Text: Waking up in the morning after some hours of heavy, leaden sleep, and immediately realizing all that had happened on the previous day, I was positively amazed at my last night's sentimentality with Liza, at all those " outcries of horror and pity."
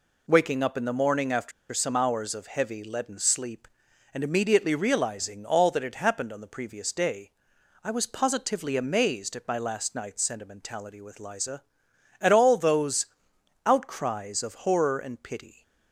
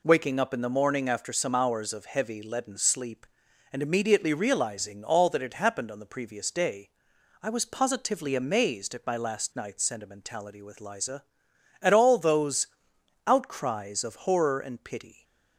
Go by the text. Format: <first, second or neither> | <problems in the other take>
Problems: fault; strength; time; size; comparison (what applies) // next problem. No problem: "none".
second | pauses between "after" and "some"; slight; at 1.5 s; 0.20 s long